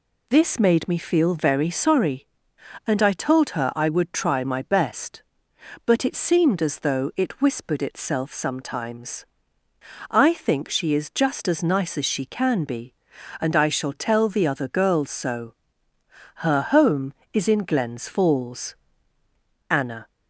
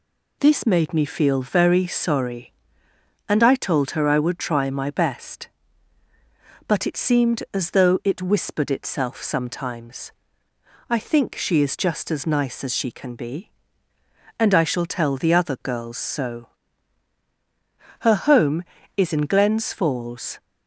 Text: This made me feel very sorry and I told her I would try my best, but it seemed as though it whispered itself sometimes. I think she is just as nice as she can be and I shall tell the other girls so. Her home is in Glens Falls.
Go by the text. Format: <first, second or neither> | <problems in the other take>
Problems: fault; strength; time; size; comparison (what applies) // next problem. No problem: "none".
second | goes on to say "Anna"; slight; from 19.6 s on; 0.38 s long